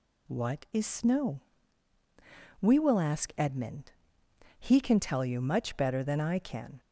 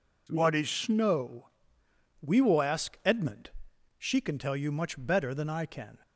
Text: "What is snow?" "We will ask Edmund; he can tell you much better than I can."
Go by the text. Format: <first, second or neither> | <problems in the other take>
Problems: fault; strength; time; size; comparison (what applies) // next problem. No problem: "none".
first | says "she" for "he"; at 3.9 s